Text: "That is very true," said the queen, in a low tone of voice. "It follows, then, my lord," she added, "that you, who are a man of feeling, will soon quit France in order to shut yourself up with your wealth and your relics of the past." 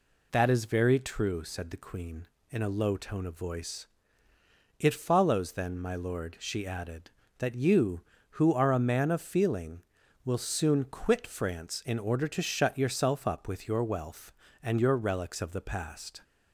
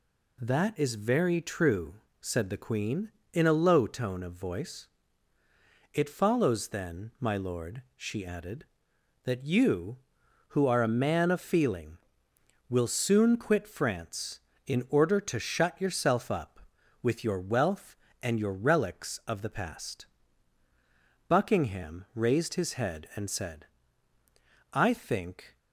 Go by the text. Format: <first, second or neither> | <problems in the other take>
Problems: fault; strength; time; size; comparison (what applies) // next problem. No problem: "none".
first | goes on to say "Buckingham raised his head and said I think"; strong; from 21.2 s on; 4.3 s long